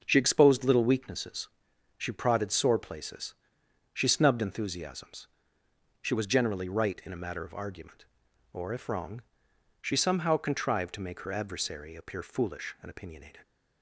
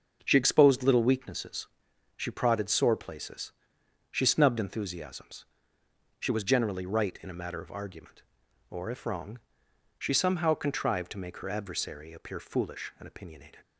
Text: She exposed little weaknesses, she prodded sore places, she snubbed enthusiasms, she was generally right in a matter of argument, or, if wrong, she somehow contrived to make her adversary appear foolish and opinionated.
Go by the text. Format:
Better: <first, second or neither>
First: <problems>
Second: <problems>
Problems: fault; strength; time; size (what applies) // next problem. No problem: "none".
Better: neither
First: starts louder than the rest; until 1.0 s; 6.5 dB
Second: starts louder than the rest; until 1.2 s; 6.5 dB